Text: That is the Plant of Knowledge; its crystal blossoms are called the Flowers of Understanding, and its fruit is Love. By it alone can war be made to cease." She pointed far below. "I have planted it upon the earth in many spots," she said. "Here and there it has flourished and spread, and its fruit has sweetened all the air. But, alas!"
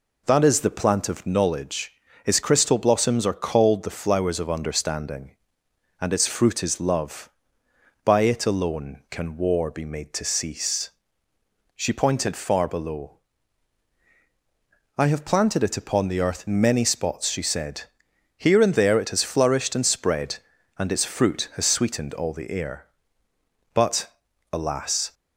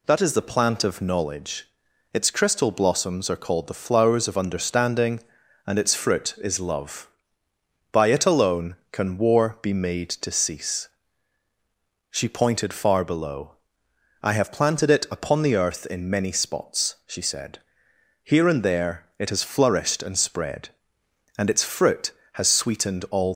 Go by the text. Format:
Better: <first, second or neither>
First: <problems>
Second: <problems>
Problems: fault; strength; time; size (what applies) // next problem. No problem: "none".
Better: first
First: none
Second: pauses between "there" and "it"; slight; at 19.0 s; 0.18 s long // stops before "the air But alas"; at 23.3 s